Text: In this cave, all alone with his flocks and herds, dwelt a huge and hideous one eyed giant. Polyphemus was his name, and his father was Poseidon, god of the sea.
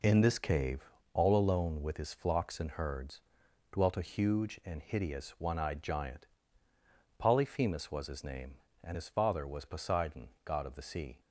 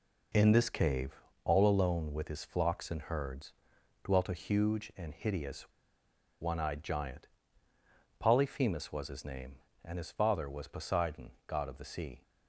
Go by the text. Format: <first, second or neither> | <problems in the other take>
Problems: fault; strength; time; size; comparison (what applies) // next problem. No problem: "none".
first | pauses between "hideous" and "one"; noticeable; at 5.6 s; 0.73 s long